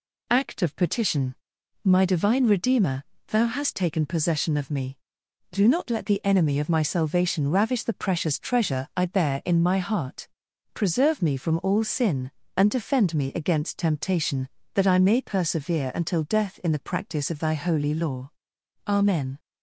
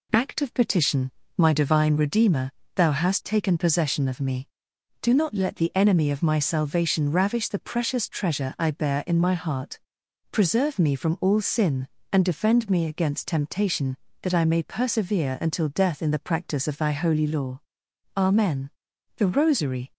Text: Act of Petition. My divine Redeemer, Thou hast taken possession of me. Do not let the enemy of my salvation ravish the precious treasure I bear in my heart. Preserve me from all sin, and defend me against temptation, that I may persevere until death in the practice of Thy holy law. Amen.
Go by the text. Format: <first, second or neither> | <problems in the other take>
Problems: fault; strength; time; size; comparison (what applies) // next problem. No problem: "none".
first | goes on to say "THE ROSARY"; noticeable; from 19.1 s on; 0.76 s long